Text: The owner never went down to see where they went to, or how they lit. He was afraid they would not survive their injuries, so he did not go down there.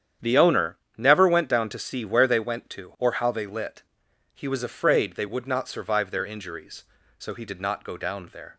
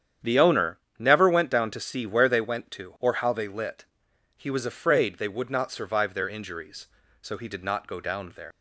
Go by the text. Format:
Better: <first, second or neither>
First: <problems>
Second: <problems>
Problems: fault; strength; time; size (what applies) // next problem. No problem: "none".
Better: first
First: starts louder than the rest; strong; until 1.4 s; 9 dB // pauses between "owner" and "never"; slight; at 0.7 s; 0.20 s long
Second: starts louder than the rest; strong; until 1.4 s; 9 dB // pauses between "owner" and "never"; slight; at 0.7 s; 0.20 s long // leaves "there" unfinished; at 8.5 s; 90 ms